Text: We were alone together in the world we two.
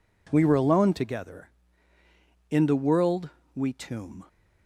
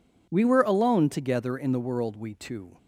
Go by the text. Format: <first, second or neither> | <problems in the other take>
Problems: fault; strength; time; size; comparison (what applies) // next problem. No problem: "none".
second | pauses between "world" and "we"; slight; at 3.2 s; 0.26 s long // says "tomb" for "two"; at 3.7 s